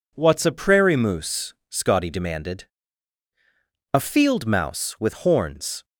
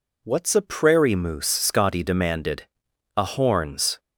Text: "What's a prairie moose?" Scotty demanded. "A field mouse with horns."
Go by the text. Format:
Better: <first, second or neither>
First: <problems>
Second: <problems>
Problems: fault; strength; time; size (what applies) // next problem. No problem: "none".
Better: first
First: none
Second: skips "field mouse with"; at 3.2 s